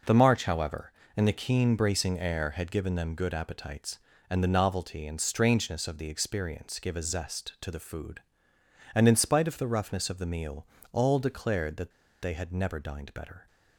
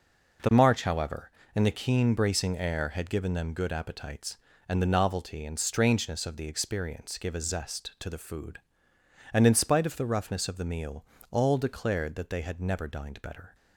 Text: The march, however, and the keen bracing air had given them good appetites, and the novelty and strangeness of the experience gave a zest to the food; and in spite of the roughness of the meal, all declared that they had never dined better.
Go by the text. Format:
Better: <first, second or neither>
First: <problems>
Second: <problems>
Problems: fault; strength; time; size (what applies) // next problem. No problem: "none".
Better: second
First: pauses between "that" and "they"; slight; at 11.9 s; 0.31 s long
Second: none